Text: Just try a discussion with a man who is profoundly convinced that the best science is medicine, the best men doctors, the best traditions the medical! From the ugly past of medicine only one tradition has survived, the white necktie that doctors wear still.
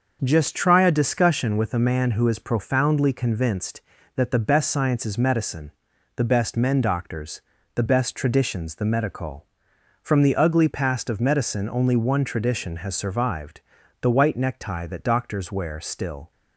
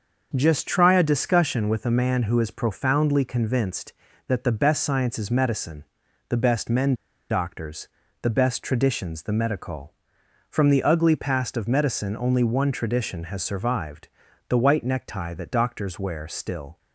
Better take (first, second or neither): first